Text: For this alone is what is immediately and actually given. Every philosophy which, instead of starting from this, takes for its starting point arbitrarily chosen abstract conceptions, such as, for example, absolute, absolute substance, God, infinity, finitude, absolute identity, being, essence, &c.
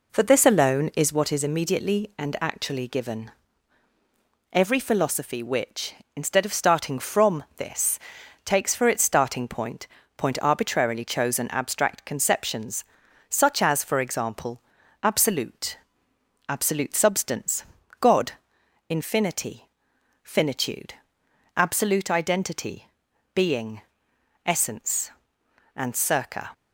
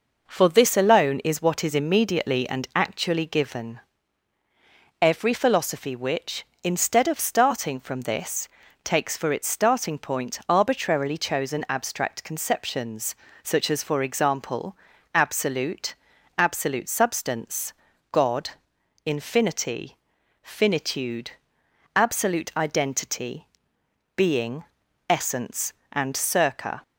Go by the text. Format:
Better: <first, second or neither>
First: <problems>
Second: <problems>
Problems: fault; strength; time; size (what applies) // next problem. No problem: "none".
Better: second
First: says "point" twice; at 10.1 s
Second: none